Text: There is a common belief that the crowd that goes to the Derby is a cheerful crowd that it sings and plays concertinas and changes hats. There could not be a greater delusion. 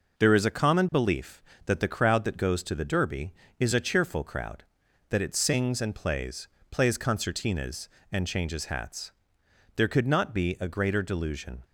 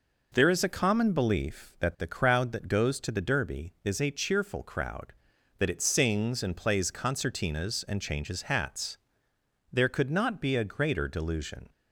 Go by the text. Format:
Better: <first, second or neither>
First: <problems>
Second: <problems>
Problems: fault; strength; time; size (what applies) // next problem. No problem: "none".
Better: second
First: says "plays" twice; at 6.7 s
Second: none